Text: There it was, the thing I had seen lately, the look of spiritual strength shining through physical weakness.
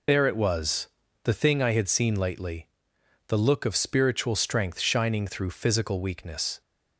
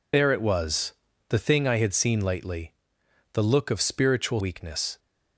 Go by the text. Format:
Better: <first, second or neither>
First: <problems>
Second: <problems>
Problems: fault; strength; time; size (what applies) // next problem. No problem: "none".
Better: first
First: none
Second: skips "strength shining through physical"; at 4.3 s